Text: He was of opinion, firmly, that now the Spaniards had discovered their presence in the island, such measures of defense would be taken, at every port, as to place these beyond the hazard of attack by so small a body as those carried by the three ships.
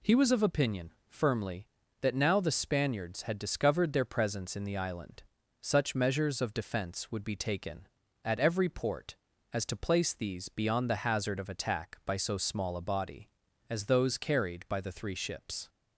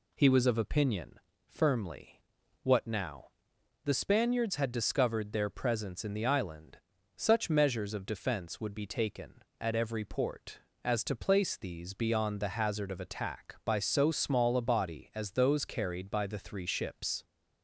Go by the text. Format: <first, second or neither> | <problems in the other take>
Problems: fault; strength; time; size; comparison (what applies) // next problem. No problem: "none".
first | says "what" for "that"; at 2.6 s // pauses between "now" and "the"; noticeable; at 3.2 s; 0.56 s long